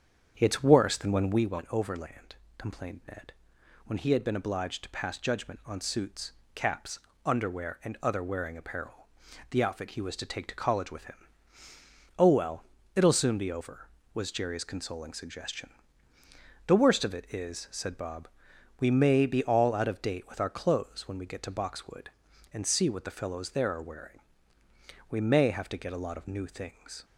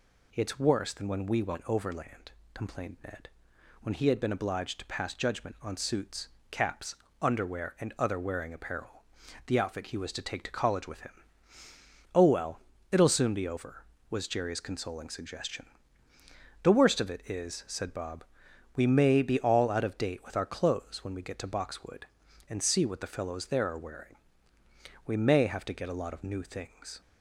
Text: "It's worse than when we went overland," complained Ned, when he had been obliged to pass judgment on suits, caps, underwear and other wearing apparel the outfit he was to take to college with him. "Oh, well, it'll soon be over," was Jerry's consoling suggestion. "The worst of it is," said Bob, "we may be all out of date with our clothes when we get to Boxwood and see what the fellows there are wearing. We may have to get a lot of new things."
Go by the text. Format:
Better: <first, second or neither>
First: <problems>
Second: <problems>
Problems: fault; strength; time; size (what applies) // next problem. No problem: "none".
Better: second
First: starts louder than the rest; strong; until 1.5 s; 8 dB // pauses between "apparel" and "the"; at 9.0 s; 0.40 s long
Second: pauses between "apparel" and "the"; at 9.0 s; 0.40 s long